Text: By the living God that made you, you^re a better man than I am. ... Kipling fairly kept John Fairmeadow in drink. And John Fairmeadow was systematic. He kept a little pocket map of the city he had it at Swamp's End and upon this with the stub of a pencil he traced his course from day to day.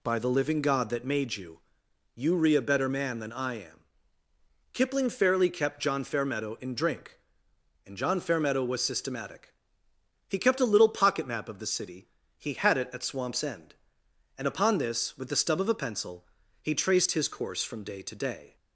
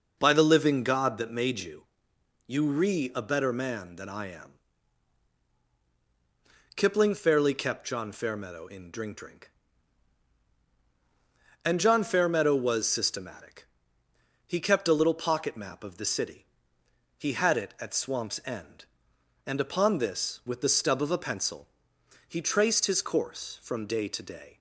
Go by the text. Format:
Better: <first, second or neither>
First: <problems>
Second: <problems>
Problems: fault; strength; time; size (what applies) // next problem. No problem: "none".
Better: first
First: pauses between "city" and "he"; slight; at 12.0 s; 0.30 s long // pauses between "pencil" and "he"; at 16.2 s; 0.38 s long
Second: says "drink" twice; at 9.1 s // pauses between "city" and "he"; noticeable; at 16.4 s; 0.74 s long // pauses between "pencil" and "he"; noticeable; at 21.6 s; 0.64 s long